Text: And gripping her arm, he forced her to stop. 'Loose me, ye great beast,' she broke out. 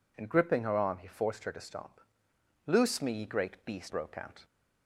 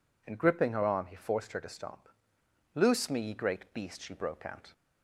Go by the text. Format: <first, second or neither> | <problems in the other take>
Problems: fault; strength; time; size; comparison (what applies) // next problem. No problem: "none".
second | skips "she"; at 3.8 s